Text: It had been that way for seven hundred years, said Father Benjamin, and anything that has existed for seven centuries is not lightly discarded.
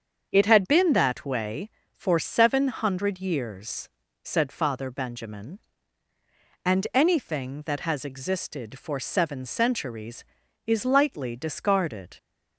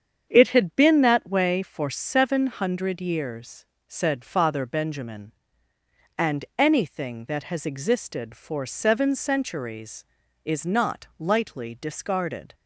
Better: second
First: starts louder than the rest; until 1.3 s; 7 dB // skips "not"; at 10.8 s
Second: starts louder than the rest; strong; until 1.3 s; 7.5 dB

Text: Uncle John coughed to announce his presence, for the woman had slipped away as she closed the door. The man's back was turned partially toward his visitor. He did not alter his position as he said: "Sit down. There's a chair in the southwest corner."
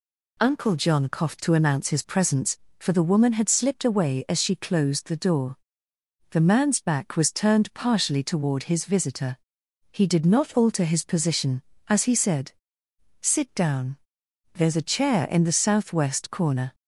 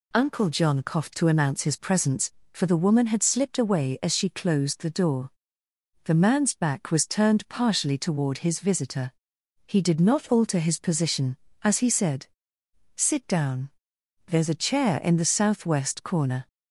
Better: neither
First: none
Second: none

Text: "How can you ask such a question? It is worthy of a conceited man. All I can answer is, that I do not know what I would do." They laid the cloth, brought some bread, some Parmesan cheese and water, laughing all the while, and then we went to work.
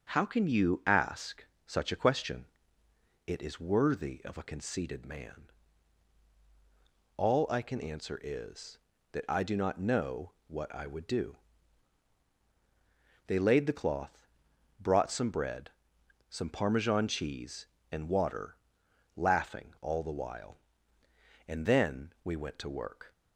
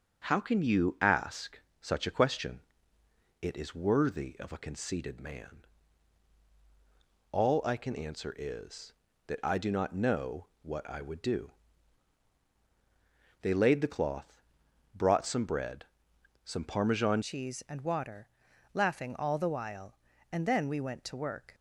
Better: first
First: starts louder than the rest; until 1.1 s; 7 dB // pauses between "ask" and "such"; slight; at 1.4 s; 0.22 s long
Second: starts louder than the rest; until 1.3 s; 7 dB // pauses between "ask" and "such"; slight; at 1.5 s; 0.22 s long // changes voice at "cheese"; from 17.2 s on; 4.3 s long

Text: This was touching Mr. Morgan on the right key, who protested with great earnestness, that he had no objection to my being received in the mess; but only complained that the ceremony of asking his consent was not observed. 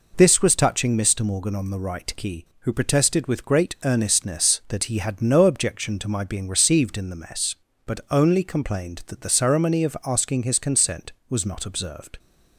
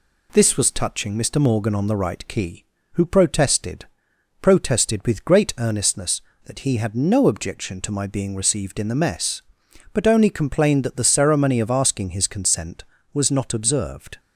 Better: first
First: none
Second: says "protested" twice; at 4.4 s

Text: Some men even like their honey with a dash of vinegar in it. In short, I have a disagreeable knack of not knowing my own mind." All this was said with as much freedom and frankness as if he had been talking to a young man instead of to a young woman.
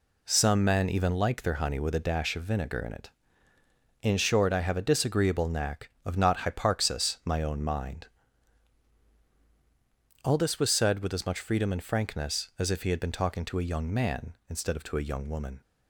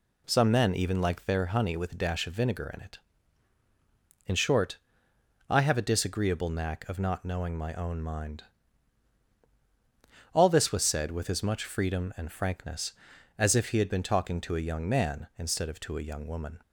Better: second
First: says "hyparxis" for "knowing"; at 6.3 s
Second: none

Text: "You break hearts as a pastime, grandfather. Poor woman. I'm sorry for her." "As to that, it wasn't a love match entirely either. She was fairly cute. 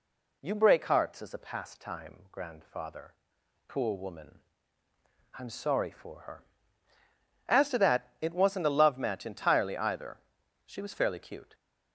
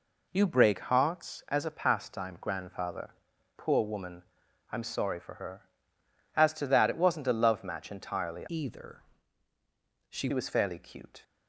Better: first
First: none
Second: changes voice from "either" to "She"; from 8.4 to 10.2 s; 1.8 s long

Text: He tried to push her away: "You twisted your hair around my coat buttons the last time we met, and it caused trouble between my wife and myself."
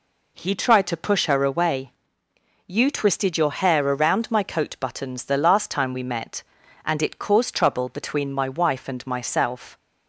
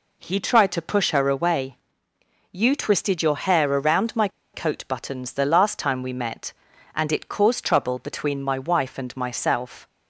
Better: first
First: none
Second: pauses between "my" and "coat"; slight; at 4.2 s; 0.25 s long

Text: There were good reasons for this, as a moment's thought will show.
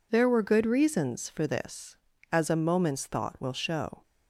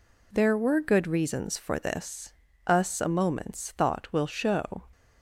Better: first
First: none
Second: says "us" for "as"; at 2.6 s

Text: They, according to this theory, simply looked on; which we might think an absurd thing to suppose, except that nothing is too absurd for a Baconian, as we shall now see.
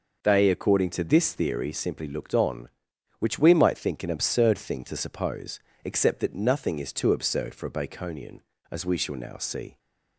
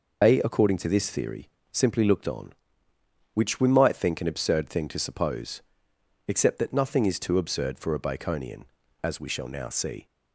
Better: first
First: none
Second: loses the start of "They"; at 0.2 s; 130 ms

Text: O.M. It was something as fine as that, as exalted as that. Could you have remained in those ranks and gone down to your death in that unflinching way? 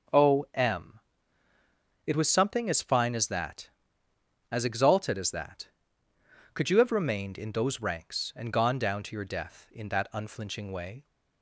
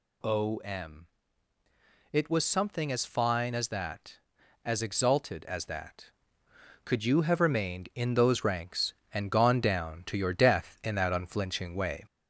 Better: first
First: none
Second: gets louder; slight; throughout; 2.5 dB

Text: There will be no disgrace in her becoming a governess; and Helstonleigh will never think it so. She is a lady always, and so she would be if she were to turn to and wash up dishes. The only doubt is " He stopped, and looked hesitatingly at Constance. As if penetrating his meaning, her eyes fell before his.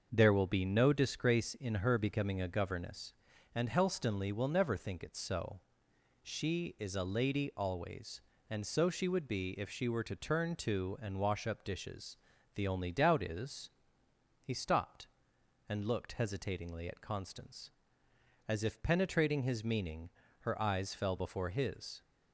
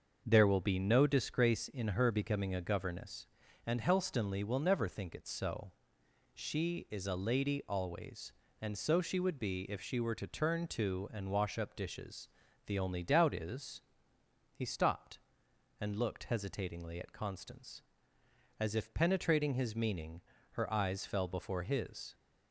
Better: neither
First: starts louder than the rest; until 1.1 s; 6.5 dB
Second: starts louder than the rest; until 1.2 s; 6.5 dB

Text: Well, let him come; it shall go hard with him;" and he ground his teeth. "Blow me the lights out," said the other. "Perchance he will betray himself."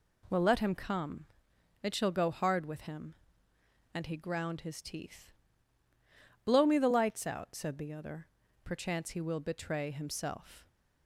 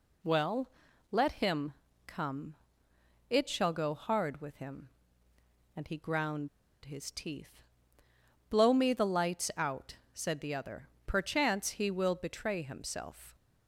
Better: first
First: none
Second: pauses between "him" and "come"; slight; at 1.7 s; 0.32 s long // pauses between "ground" and "his"; at 6.4 s; 0.36 s long

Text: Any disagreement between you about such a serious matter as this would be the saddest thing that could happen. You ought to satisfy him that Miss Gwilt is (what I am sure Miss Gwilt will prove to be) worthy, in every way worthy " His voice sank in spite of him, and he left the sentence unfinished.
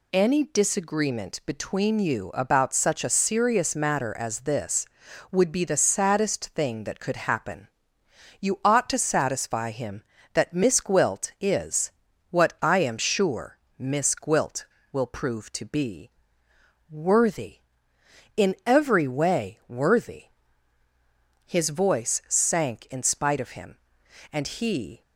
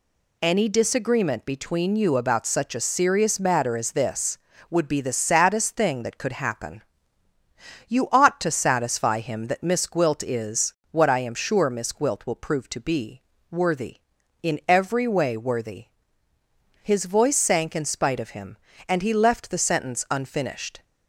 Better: second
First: pauses between "sure" and "Miss"; slight; at 13.5 s; 0.20 s long // stops before "left the sentence unfinished"; at 25.0 s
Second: none

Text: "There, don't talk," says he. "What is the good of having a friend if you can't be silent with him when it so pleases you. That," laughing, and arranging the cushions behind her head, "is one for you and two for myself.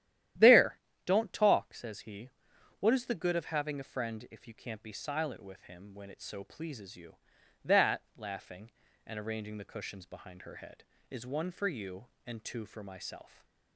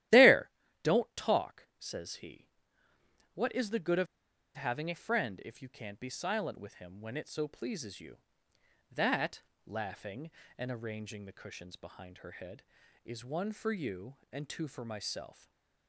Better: first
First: starts louder than the rest; strong; until 1.6 s; 12 dB // stays silent after the last word; slight; from 13.2 s on; 0.5 s long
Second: starts louder than the rest; strong; until 1.4 s; 13.5 dB // pauses between "of" and "having"; noticeable; at 4.0 s; 0.49 s long // stays silent after the last word; slight; from 15.3 s on; 0.5 s long

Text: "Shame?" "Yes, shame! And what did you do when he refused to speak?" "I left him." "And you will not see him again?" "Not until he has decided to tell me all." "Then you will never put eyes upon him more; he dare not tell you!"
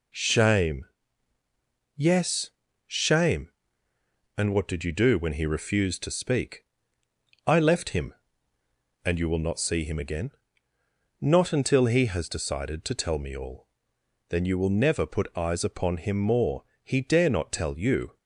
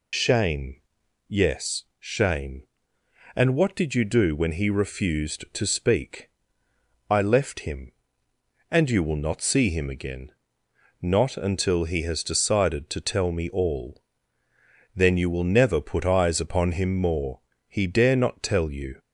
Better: first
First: none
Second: loses the start of "Shame"; at 0.1 s; 75 ms

